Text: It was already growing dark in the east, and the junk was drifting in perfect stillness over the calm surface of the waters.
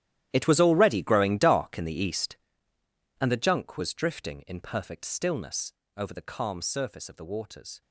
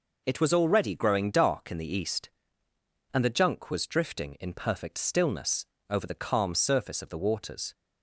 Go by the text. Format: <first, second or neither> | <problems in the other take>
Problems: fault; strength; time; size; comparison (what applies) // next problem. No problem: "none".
second | gets quieter; strong; throughout; 16.5 dB // pauses between "stillness" and "over"; slight; at 5.7 s; 0.24 s long; slight in the second